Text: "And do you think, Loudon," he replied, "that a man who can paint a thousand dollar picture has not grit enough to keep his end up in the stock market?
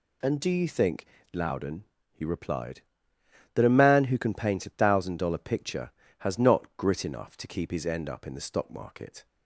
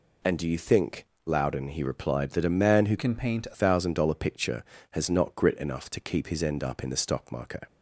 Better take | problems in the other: first | changes voice from "can" to "a"; from 2.9 to 3.5 s; 0.6 s long

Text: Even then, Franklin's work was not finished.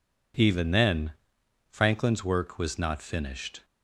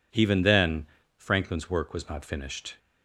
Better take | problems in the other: neither | none

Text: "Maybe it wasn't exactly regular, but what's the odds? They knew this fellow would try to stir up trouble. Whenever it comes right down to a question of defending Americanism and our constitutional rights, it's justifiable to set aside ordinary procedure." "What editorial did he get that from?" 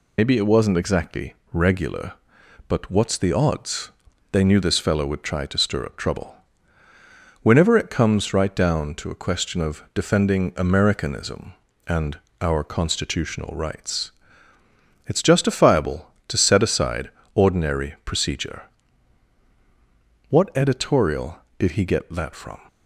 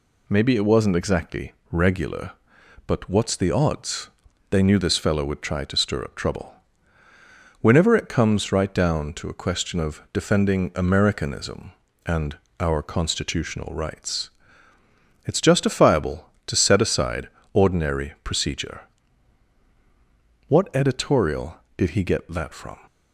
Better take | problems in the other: second | loses the start of "Maybe"; at 0.1 s; 80 ms // pauses between "exactly" and "regular"; slight; at 1.3 s; 0.18 s long; slight in the second // pauses between "and" and "our"; slight; at 12.1 s; 0.22 s long; slight in the second // pauses between "aside" and "ordinary"; slight; at 17.1 s; 0.24 s long; slight in the second

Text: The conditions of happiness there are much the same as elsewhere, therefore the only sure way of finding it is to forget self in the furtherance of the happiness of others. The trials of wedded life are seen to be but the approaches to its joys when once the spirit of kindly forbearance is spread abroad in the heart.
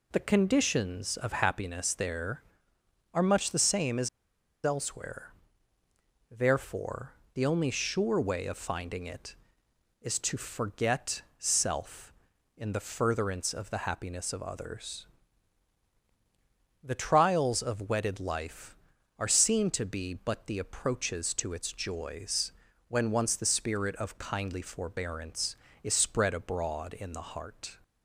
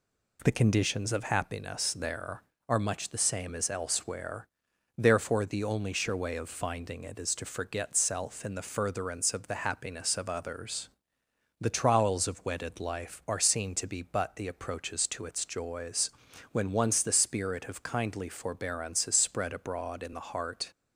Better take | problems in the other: second | pauses between "as" and "elsewhere"; noticeable; at 4.0 s; 0.55 s long // pauses between "therefore" and "the"; slight; at 7.1 s; 0.22 s long // pauses between "forget" and "self"; slight; at 11.2 s; 0.16 s long // pauses between "joys" and "when"; at 22.5 s; 0.38 s long; also in the second

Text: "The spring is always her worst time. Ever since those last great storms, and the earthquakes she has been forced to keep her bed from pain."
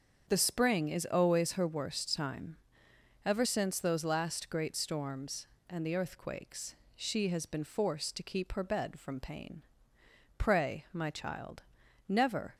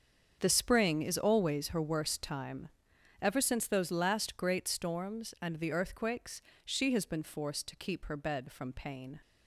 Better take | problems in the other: second | starts louder than the rest; until 1.2 s; 7 dB; strong in the second // pauses between "earthquakes" and "she"; slight; at 6.7 s; 0.20 s long; slight in the second // goes on to say "Pray my child Never"; strong; from 10.3 s on; 2.1 s long

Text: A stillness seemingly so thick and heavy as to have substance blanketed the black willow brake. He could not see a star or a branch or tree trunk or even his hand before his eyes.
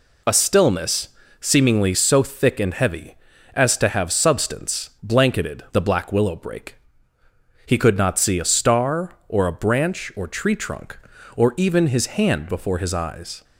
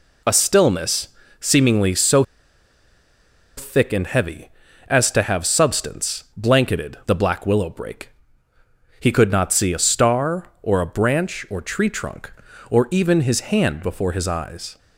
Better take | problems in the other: first | pauses between "stillness" and "seemingly"; slight; at 1.0 s; 0.32 s long; slight in the first // pauses between "so" and "thick"; strong; at 2.2 s; 1.3 s long

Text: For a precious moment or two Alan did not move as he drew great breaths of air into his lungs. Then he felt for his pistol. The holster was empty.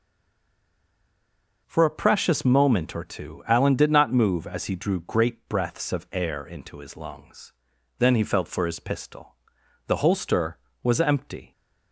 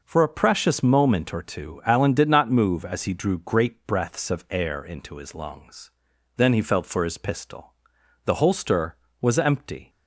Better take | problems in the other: second | stays silent before the first word; noticeable; until 1.6 s; 1.6 s long

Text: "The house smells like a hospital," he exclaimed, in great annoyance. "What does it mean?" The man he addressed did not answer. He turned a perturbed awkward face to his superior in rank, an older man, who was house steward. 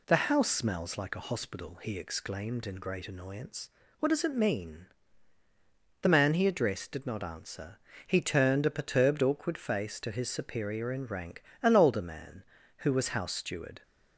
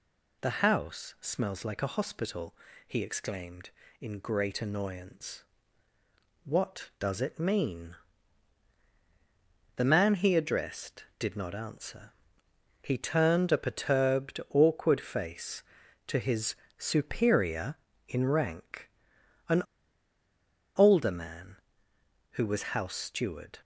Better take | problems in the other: first | pauses between "his" and "superior"; slight; at 16.5 s; 0.22 s long // pauses between "an" and "older"; at 19.6 s; 1.1 s long

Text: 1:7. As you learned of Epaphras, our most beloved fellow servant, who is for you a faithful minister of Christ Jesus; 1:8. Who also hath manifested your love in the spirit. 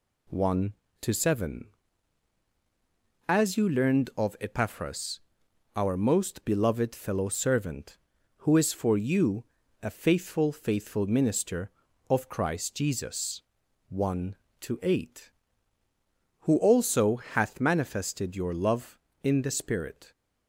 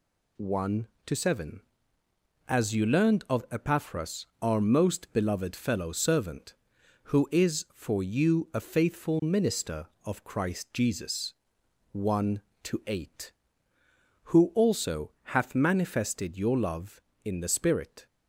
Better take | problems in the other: second | pauses between "you" and "a"; slight; at 9.4 s; 0.36 s long // says "faithful" twice; at 10.5 s

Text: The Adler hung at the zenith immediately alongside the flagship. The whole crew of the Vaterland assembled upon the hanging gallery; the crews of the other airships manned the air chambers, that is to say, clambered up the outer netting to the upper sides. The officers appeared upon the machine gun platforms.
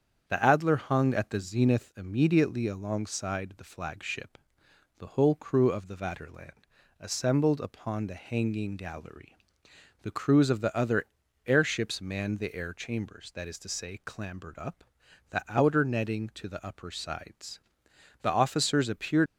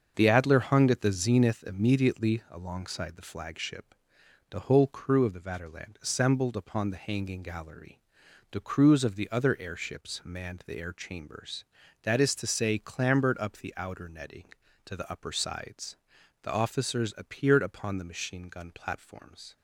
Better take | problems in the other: second | starts louder than the rest; strong; until 1.2 s; 8 dB; also in the second // pauses between "Vaterland" and "assembled"; at 6.5 s; 0.42 s long // pauses between "other" and "airships"; at 11.0 s; 0.40 s long // pauses between "up" and "the"; noticeable; at 14.8 s; 0.46 s long // stops before "upon the machine gun platforms"; at 19.2 s

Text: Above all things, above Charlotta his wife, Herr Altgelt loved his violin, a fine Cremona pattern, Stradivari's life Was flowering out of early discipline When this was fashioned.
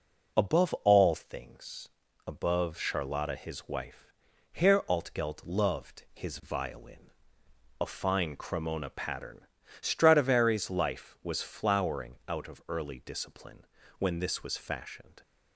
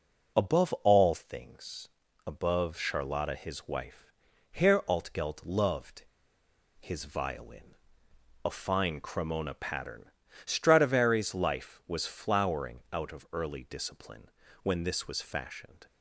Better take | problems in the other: first | pauses between "loved" and "his"; noticeable; at 6.0 s; 0.75 s long // pauses between "discipline" and "When"; slight; at 14.2 s; 0.34 s long; slight in the first

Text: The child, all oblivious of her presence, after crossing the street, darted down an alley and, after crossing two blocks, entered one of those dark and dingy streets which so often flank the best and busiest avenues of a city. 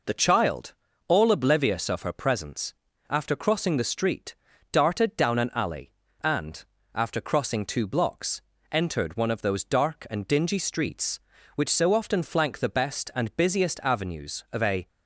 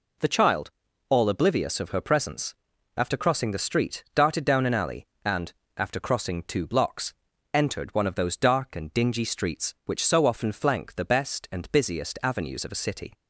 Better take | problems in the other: second | stops before "city"; at 14.8 s

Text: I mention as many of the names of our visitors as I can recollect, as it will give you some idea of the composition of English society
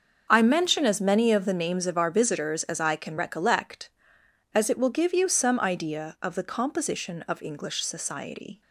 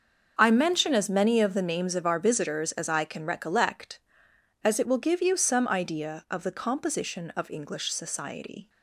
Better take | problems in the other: neither | starts louder than the rest; the same in both

